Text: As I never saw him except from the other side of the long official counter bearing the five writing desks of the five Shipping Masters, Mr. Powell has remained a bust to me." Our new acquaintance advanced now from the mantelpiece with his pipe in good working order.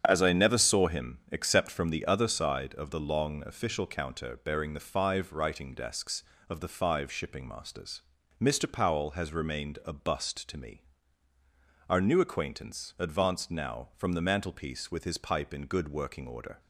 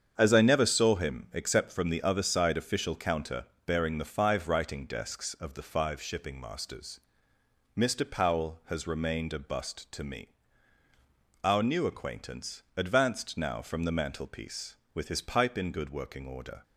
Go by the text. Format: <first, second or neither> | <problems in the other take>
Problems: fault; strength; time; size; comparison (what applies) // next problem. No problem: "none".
first | starts louder than the rest; strong; until 1.1 s; 7.5 dB; strong in the first // skips "of the long"; at 2.5 s // pauses between "counter" and "bearing"; slight; at 3.4 s; 0.22 s long // pauses between "acquaintance" and "advanced"; slight; at 12.6 s; 0.16 s long